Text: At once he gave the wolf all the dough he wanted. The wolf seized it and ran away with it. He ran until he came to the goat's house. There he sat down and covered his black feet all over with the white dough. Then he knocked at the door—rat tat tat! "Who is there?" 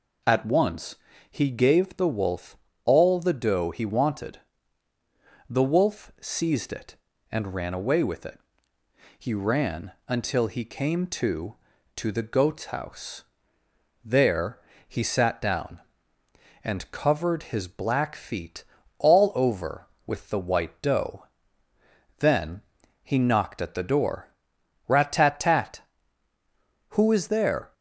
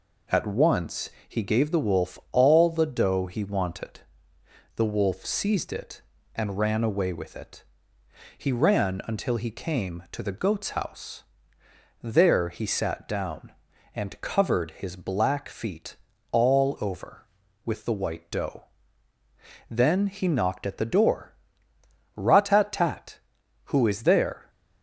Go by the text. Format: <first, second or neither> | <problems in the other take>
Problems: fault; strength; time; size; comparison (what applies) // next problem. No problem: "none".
second | pauses between "once" and "he"; slight; at 0.9 s; 0.34 s long; slight in the second // pauses between "wolf" and "all"; slight; at 2.5 s; 0.28 s long // pauses between "ran" and "until"; slight; at 9.9 s; 0.16 s long // says "to" twice; at 11.9 s // pauses between "There" and "he"; slight; at 14.5 s; 0.28 s long // pauses between "feet" and "all"; slight; at 18.6 s; 0.36 s long; slight in the second // pauses between "Then" and "he"; at 22.6 s; 0.42 s long